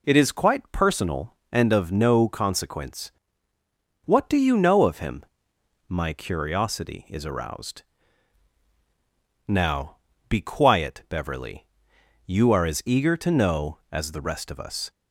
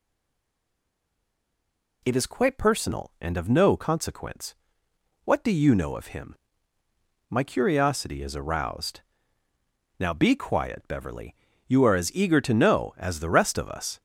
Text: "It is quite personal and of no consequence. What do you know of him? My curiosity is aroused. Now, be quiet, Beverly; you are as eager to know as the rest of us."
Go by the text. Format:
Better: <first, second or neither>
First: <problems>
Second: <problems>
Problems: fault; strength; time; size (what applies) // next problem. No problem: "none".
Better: first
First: none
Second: stays silent before the first word; noticeable; until 2.0 s; 2.0 s long